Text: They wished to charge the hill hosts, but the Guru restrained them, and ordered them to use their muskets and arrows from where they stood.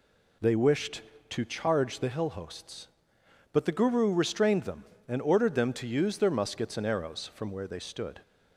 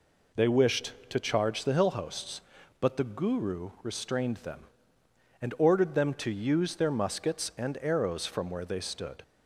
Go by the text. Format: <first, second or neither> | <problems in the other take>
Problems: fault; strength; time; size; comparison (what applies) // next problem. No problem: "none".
neither | none